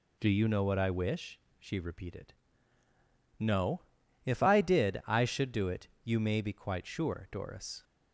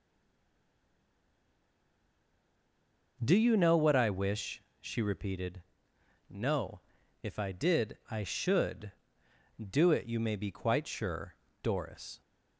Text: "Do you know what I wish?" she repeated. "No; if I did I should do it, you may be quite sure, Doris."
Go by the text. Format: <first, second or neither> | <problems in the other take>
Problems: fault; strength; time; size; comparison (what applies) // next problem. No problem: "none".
first | stays silent before the first word; strong; until 3.1 s; 3.1 s long